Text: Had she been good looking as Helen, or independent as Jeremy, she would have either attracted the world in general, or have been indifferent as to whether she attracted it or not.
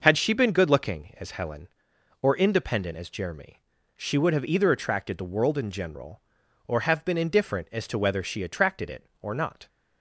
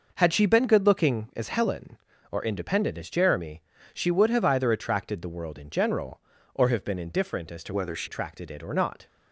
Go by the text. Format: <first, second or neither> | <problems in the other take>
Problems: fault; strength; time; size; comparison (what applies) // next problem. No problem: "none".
first | changes voice from "whether" to "she"; from 7.7 to 8.0 s; 0.3 s long